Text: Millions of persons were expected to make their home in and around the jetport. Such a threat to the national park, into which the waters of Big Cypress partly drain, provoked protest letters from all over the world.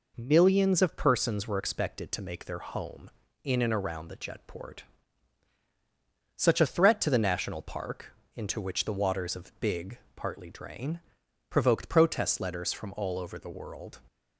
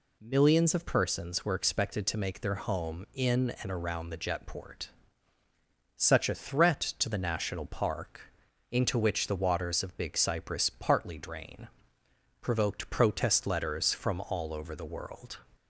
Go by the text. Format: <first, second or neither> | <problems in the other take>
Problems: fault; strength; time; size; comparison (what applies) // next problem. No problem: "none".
second | skips "Cypress"; at 10.0 s